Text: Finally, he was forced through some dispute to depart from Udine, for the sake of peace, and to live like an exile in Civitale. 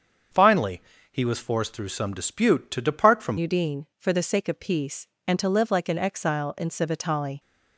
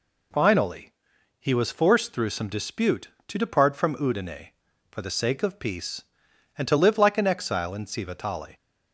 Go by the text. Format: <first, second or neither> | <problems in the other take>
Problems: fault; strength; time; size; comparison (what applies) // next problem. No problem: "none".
second | starts louder than the rest; until 1.6 s; 7 dB // changes voice at "Udine"; from 3.3 s on; 4.0 s long